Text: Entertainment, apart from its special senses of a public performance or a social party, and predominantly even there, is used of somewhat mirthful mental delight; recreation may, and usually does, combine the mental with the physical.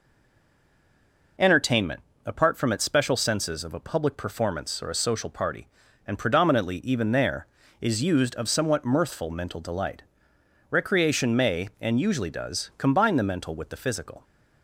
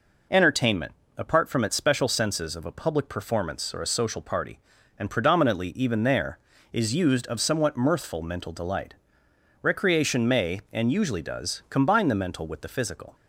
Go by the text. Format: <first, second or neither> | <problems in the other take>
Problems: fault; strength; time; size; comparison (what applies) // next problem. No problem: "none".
second | stays silent before the first word; noticeable; until 1.3 s; 1.3 s long